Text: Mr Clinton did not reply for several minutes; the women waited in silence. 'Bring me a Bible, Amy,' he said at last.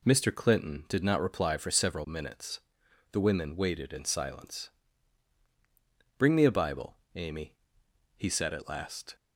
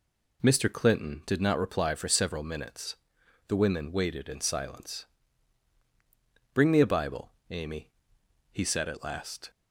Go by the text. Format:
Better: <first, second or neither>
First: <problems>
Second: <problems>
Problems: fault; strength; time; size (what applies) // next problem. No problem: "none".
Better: neither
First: none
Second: none